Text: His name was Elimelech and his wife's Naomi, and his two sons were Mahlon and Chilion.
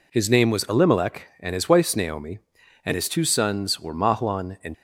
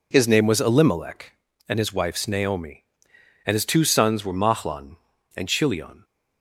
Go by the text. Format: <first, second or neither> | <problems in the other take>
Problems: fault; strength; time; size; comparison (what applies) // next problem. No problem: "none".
second | stops before "Chilion"; at 4.7 s